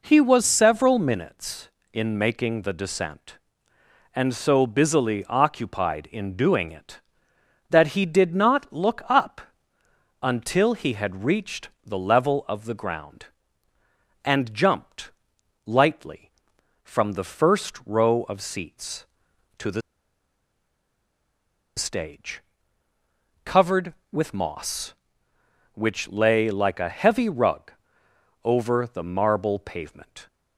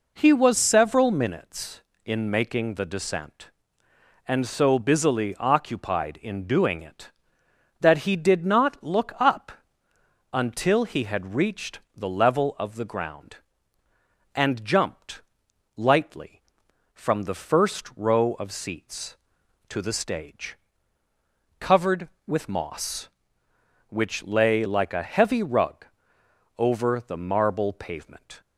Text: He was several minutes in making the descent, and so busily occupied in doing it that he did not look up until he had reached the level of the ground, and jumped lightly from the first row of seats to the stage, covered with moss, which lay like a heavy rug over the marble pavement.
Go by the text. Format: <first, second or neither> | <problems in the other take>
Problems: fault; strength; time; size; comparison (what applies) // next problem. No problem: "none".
second | pauses between "up" and "until"; noticeable; at 9.4 s; 0.80 s long; noticeable in the second // pauses between "reached" and "the"; slight; at 11.6 s; 0.16 s long; slight in the second // pauses between "jumped" and "lightly"; noticeable; at 15.1 s; 0.54 s long; noticeable in the second // pauses between "the" and "stage"; strong; at 19.8 s; 1.9 s long // pauses between "rug" and "over"; noticeable; at 27.7 s; 0.72 s long; noticeable in the second